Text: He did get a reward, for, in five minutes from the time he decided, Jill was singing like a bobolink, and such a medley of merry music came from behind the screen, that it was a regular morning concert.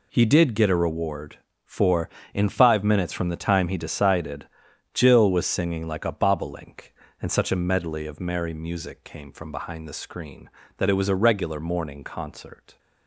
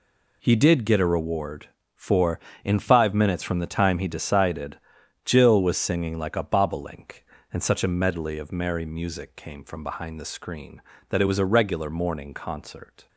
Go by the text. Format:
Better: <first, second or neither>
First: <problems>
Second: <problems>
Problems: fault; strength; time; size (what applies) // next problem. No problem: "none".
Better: neither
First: none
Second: none